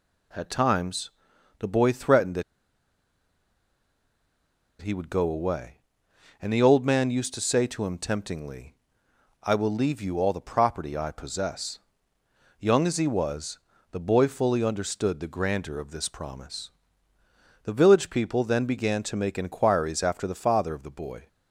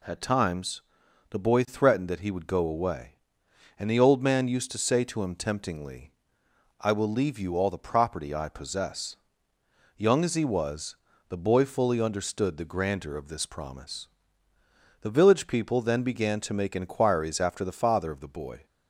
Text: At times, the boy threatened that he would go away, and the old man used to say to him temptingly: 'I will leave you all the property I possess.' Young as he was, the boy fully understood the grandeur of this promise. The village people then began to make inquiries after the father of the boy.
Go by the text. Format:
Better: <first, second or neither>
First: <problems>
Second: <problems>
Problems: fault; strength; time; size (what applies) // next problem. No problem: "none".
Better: second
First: pauses between "that" and "he"; strong; at 2.4 s; 2.3 s long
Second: none